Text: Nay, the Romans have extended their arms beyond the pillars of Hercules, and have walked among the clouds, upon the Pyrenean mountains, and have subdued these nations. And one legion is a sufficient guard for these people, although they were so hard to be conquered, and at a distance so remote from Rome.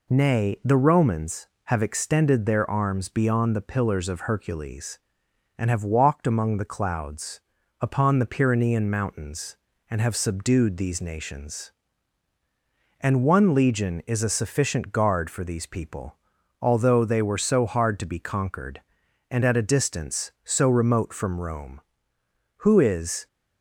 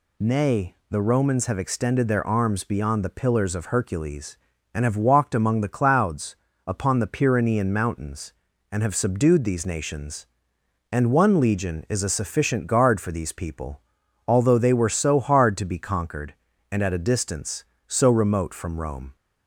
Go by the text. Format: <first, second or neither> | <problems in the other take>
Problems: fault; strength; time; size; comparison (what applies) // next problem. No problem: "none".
second | goes on to say "Who is"; noticeable; from 22.6 s on; 0.64 s long